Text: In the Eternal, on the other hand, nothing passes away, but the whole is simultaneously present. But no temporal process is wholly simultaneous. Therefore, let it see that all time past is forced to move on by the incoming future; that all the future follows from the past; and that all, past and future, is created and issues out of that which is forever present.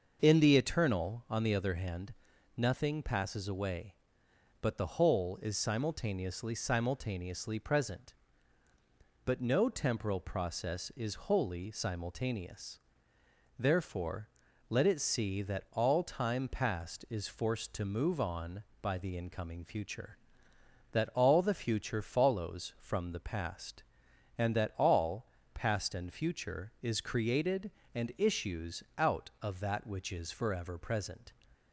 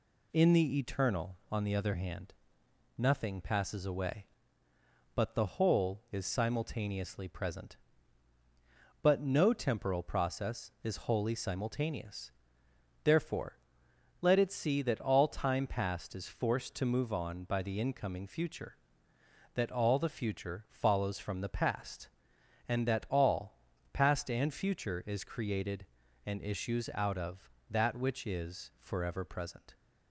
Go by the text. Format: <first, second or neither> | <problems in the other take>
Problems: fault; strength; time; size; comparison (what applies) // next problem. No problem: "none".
second | starts louder than the rest; noticeable; until 1.2 s; 6 dB // says "simultaneously" twice; at 6.5 s